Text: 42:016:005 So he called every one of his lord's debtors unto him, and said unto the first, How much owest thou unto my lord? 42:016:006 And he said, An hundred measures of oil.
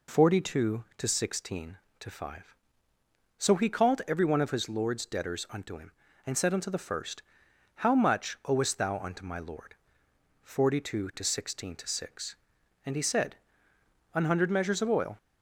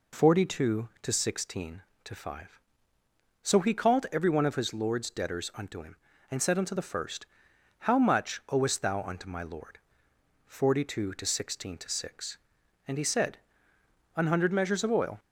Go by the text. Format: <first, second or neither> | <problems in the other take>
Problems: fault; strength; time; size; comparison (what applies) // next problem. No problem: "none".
neither | none